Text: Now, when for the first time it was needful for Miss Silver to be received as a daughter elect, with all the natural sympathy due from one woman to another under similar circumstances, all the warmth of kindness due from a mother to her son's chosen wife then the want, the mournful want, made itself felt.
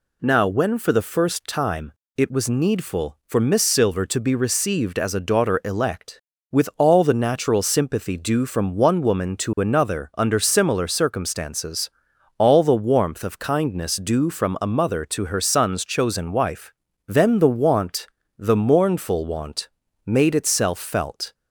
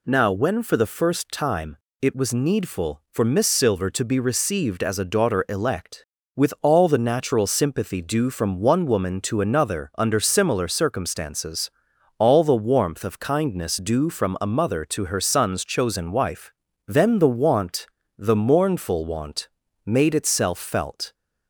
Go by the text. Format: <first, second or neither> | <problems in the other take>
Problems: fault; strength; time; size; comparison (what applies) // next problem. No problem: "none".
neither | pauses between "time" and "it"; slight; the same in both // pauses between "wife" and "then"; slight; the same in both